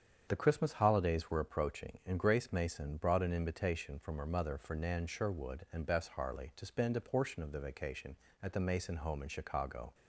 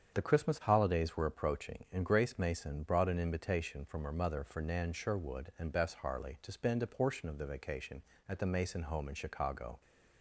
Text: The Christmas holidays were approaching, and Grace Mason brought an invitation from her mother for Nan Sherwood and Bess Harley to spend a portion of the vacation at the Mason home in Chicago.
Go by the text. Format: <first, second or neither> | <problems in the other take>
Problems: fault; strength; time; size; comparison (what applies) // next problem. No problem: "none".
neither | starts louder than the rest; strong; the same in both